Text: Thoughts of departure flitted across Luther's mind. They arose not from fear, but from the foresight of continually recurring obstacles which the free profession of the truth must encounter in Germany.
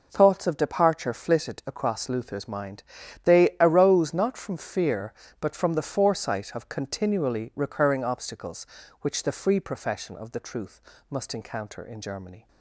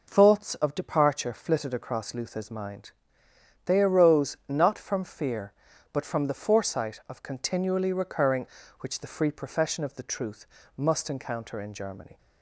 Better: first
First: pauses between "truth" and "must"; slight; at 10.8 s; 0.28 s long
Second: skips "obstacles"; at 8.6 s // pauses between "truth" and "must"; slight; at 10.4 s; 0.28 s long

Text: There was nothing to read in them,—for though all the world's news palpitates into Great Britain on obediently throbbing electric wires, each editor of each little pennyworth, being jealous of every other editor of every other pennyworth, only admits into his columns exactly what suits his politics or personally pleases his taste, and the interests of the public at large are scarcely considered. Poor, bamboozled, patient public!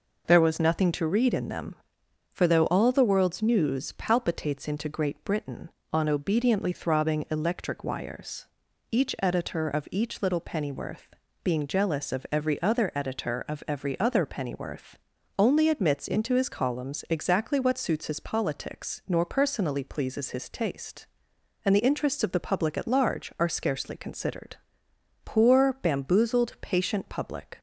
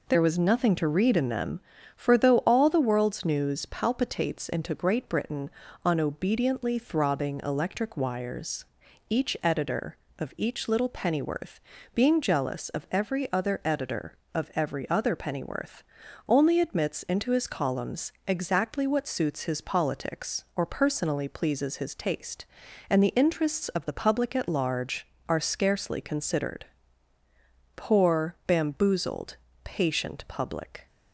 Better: second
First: says "nor" for "or"; at 19.0 s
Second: none

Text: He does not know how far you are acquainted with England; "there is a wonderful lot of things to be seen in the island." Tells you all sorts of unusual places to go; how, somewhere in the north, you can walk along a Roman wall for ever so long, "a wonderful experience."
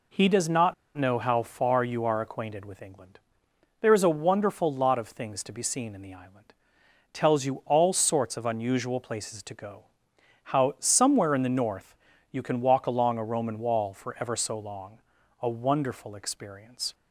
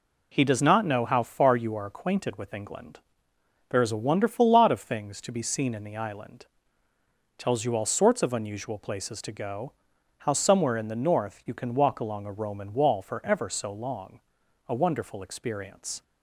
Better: second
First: pauses between "not" and "know"; slight; at 0.7 s; 0.23 s long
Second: none

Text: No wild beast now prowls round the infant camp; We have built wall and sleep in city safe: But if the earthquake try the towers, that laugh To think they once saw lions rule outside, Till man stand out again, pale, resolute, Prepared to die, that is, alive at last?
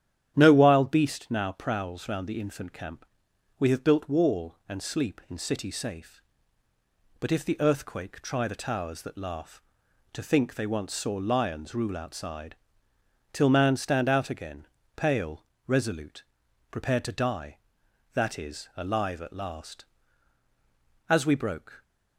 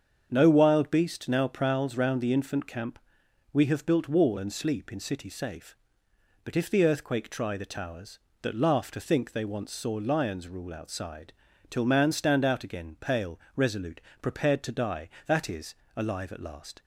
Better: second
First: starts louder than the rest; strong; until 1.3 s; 10.5 dB // goes on to say "As we broke"; noticeable; from 21.1 s on; 0.72 s long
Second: starts louder than the rest; strong; until 1.3 s; 7 dB

